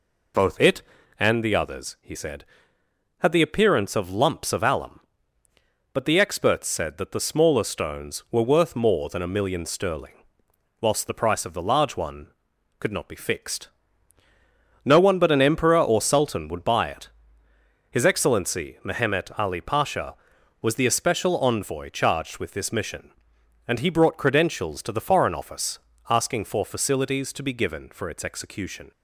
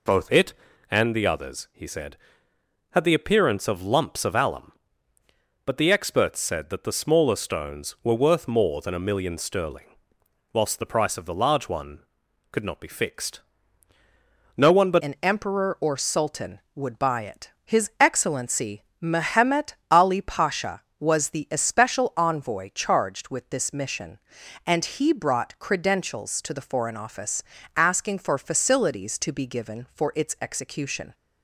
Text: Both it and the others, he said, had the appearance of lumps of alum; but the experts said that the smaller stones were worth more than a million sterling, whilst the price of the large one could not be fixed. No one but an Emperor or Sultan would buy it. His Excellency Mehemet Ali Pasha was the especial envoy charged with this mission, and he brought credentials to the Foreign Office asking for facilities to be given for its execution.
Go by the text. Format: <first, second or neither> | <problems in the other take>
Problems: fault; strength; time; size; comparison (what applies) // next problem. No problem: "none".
first | changes voice at "an"; from 14.9 s on; 16.2 s long // pauses between "Excellency" and "Mehemet"; slight; at 18.8 s; 0.18 s long // pauses between "Mehemet" and "Ali"; slight; at 19.7 s; 0.16 s long // pauses between "Office" and "asking"; slight; at 27.4 s; 0.32 s long; slight in the first